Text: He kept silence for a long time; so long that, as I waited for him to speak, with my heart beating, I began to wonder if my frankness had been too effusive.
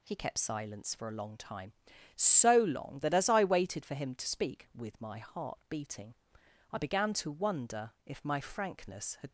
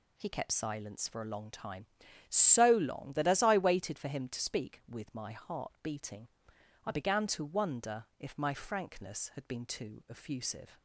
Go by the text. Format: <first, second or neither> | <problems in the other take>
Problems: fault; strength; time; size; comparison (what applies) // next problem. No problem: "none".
second | stops before "been too effusive"; at 9.2 s